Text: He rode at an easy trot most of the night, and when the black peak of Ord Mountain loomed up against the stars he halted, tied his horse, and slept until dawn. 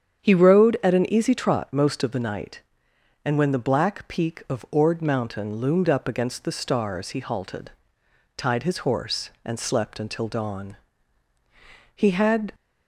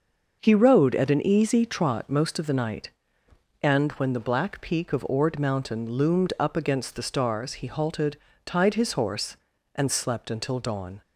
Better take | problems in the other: second | starts louder than the rest; strong; until 1.2 s; 8 dB; also in the second // goes on to say "He had"; from 11.9 s on; 0.58 s long

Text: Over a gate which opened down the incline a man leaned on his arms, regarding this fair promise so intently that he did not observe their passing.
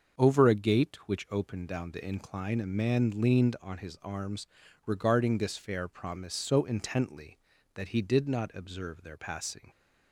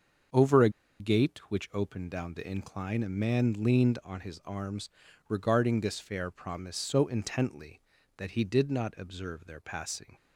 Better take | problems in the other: first | starts louder than the rest; until 1.8 s; 7 dB; also in the first // pauses between "a" and "gate"; slight; at 0.6 s; 0.30 s long

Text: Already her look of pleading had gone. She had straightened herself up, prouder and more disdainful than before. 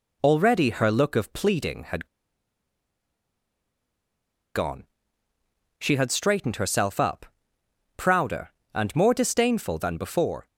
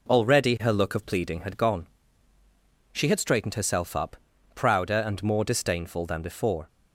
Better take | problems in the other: second | pauses between "had" and "gone"; strong; at 2.0 s; 2.4 s long

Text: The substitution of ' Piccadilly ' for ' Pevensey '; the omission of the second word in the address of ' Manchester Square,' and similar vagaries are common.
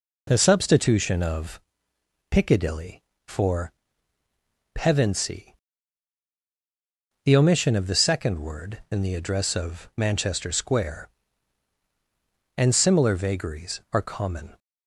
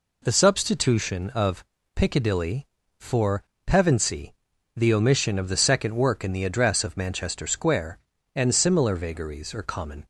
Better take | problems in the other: first | says "work" for "word"; at 5.9 s

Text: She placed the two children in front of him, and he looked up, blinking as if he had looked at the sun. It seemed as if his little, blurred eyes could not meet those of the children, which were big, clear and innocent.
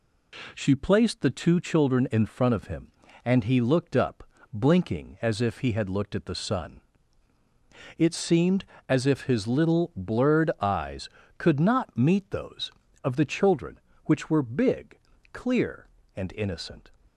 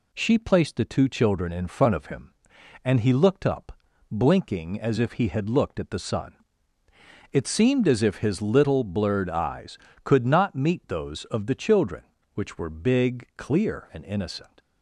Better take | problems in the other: neither | none

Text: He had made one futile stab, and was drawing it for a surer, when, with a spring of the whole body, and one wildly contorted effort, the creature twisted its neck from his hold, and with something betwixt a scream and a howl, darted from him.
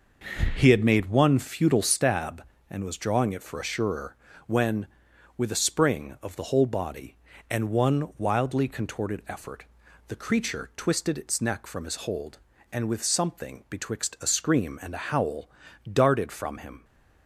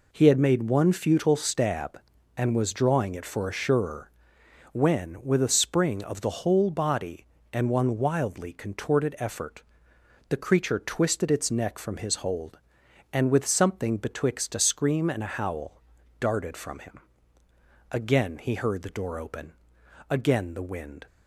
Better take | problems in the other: first | goes on to say "Again he heard the door open again the wind"; strong; from 17.8 s on; 3.1 s long

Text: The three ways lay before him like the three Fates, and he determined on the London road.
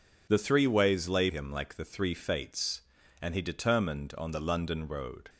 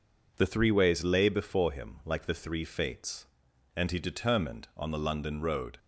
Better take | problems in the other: second | skips "before"; at 1.2 s

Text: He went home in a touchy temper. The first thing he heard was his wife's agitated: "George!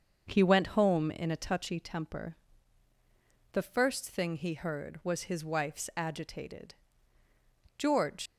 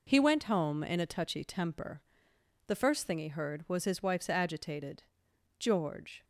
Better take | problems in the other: second | starts louder than the rest; until 1.2 s; 6.5 dB // leaves "George" unfinished; at 8.2 s; 120 ms

